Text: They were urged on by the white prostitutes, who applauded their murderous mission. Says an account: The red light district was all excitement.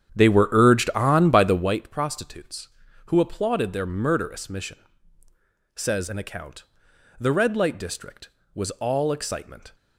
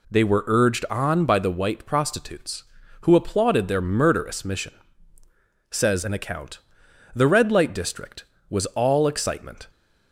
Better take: second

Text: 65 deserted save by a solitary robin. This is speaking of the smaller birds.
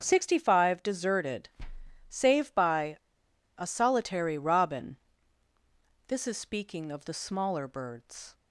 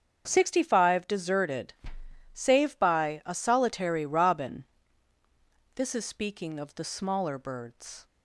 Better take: second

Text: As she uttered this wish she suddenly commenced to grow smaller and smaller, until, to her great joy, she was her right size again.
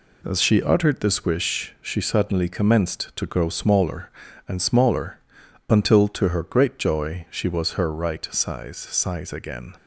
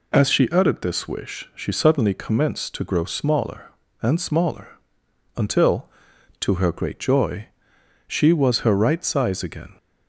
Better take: second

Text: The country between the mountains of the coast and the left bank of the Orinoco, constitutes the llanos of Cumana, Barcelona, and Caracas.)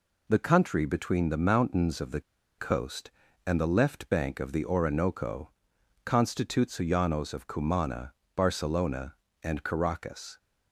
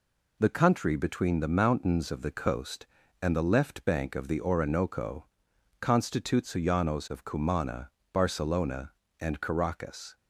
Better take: second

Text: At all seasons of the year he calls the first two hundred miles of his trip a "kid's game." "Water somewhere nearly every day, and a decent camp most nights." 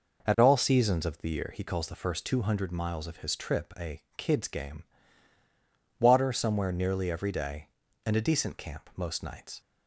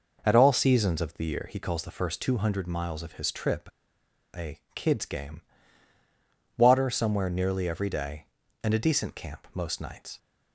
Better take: first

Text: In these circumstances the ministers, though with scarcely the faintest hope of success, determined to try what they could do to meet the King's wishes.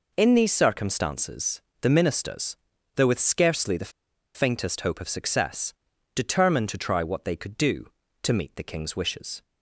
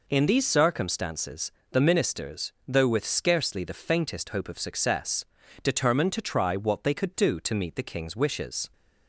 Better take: second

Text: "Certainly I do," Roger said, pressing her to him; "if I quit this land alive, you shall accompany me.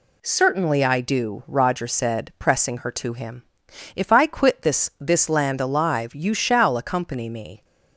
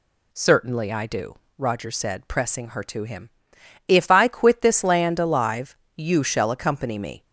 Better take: second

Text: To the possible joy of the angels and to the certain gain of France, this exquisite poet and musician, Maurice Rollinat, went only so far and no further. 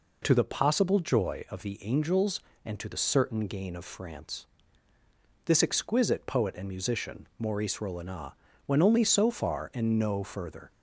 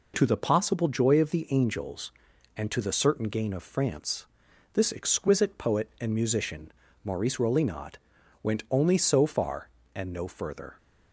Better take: neither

